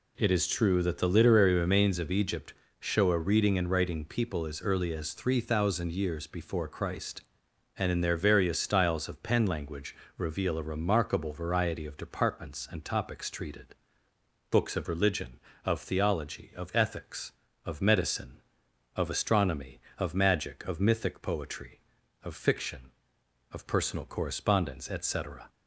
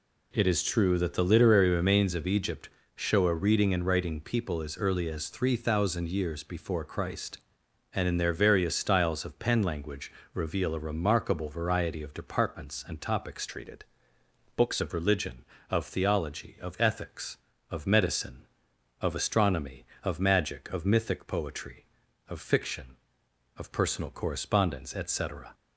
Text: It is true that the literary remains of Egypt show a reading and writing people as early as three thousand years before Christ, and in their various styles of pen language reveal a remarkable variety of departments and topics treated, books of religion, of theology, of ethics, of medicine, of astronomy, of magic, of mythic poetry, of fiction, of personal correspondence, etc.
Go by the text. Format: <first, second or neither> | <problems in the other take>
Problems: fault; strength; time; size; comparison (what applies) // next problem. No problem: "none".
first | pauses between "Egypt" and "show"; slight; at 2.6 s; 0.26 s long; slight in the first // pauses between "language" and "reveal"; slight; at 10.0 s; 0.22 s long; slight in the first // changes voice from "treated" to "books"; from 13.4 to 14.7 s; 1.3 s long